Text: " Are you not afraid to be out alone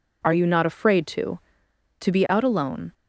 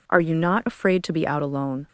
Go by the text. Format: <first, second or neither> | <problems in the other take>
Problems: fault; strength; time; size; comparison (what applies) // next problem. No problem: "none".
second | says "to" twice; at 1.9 s